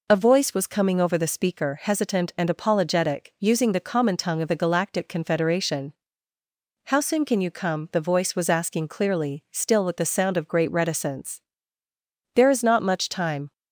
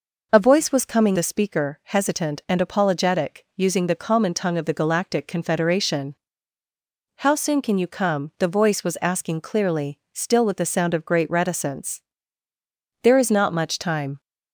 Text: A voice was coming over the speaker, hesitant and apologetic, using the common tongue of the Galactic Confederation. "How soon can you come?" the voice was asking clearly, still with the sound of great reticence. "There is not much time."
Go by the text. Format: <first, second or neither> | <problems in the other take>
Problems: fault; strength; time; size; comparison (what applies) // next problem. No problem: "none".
first | skips "over"; at 1.1 s